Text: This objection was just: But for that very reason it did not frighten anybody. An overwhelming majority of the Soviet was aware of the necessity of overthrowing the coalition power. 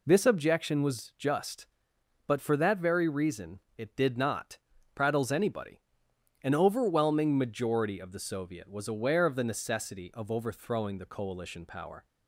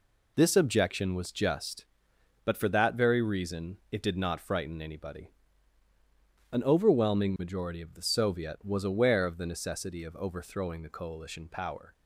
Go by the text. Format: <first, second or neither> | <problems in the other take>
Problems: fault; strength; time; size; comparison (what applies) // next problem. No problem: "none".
second | pauses between "reason" and "it"; slight; at 3.5 s; 0.18 s long // says "prattles" for "frighten"; at 4.9 s